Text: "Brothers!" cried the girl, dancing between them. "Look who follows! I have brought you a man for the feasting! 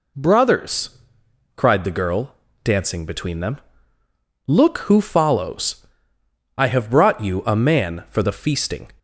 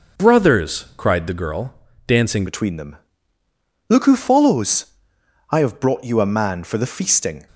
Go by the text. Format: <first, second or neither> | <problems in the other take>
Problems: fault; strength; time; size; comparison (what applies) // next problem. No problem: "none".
first | changes voice at "between"; from 2.4 s on; 5.0 s long